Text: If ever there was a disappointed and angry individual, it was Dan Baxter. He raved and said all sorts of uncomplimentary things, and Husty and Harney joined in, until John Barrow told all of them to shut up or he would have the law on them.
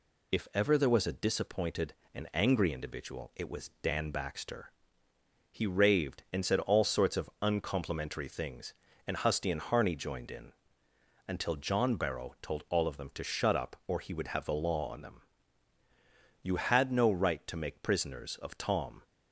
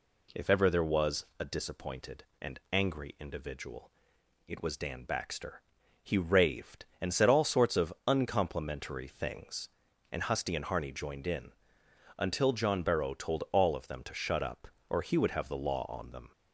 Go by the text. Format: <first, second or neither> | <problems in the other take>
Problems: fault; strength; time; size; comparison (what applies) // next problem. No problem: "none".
second | goes on to say "You had no right to make prisoners of Tom"; strong; from 16.4 s on; 2.6 s long